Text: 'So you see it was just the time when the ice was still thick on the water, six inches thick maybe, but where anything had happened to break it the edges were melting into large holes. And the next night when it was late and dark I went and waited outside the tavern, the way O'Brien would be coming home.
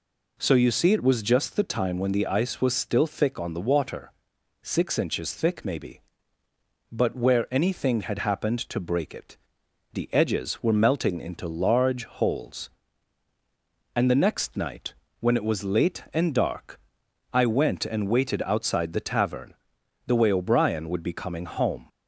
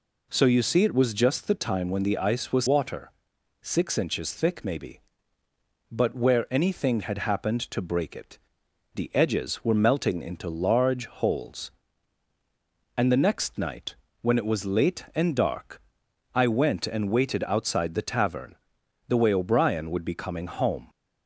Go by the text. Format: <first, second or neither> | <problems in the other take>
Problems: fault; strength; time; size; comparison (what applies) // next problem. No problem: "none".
first | skips "still thick on the"; at 2.6 s // pauses between "it" and "the"; noticeable; at 8.3 s; 0.56 s long; noticeable in the first // pauses between "night" and "when"; slight; at 13.9 s; 0.28 s long; slight in the first // pauses between "dark" and "I"; noticeable; at 15.7 s; 0.54 s long; noticeable in the first